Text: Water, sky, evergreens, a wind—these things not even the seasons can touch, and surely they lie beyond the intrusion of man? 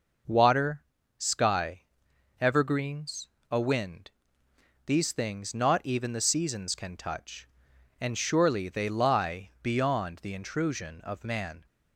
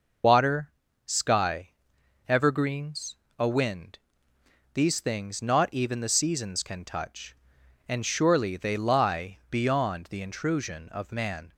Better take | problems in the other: first | loses the start of "Water"; at 0.2 s; 115 ms

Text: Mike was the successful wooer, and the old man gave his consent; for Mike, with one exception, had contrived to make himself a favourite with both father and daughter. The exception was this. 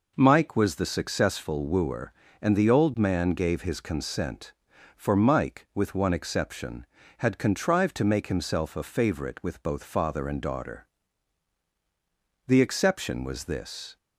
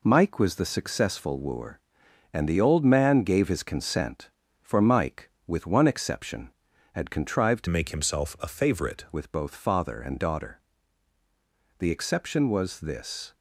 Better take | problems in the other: first | changes voice from "make" to "favourite"; from 7.6 to 9.0 s; 1.4 s long

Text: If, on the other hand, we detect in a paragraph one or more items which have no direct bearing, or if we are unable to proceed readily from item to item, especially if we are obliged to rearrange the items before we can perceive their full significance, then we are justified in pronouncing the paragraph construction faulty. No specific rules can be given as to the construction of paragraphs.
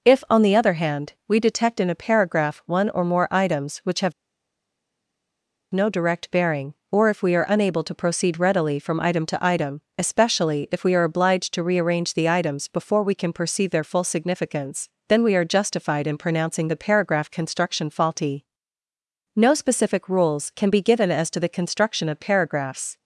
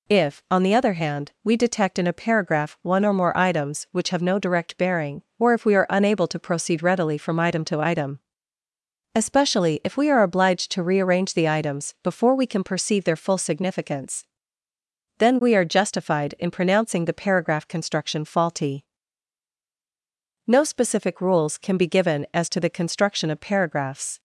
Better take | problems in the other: second | pauses between "have" and "no"; strong; at 4.1 s; 1.6 s long

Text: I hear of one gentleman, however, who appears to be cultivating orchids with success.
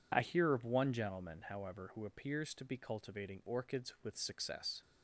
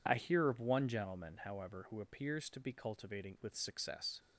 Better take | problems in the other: first | skips "orchids"; at 3.3 s

